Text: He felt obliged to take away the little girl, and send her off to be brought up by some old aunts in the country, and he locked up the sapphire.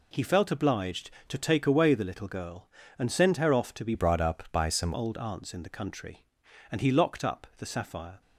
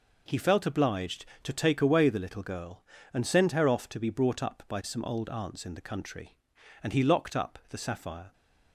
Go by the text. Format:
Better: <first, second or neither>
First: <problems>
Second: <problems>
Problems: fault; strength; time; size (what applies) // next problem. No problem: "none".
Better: second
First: changes voice from "brought" to "some"; from 3.9 to 4.9 s; 1.0 s long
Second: none